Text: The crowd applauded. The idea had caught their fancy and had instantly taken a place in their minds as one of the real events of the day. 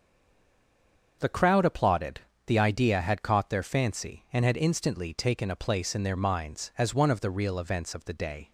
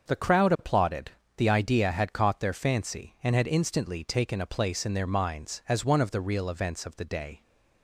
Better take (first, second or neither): second